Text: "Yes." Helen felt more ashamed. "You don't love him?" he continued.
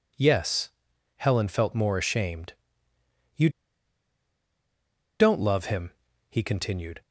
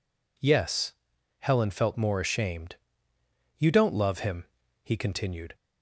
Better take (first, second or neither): second